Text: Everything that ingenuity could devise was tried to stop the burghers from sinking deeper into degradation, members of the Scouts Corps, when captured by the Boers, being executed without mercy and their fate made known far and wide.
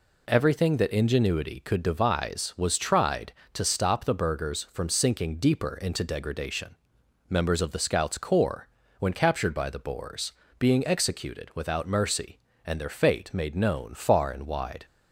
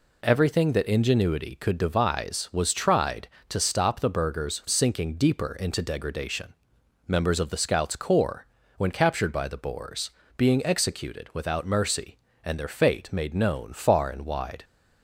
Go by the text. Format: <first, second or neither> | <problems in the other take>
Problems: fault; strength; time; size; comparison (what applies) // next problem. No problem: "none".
first | skips "from"; at 4.6 s